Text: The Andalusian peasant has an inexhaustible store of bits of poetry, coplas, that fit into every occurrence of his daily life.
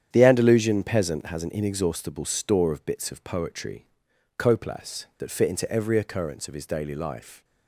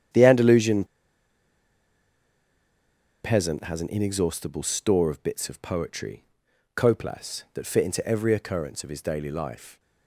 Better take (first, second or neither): first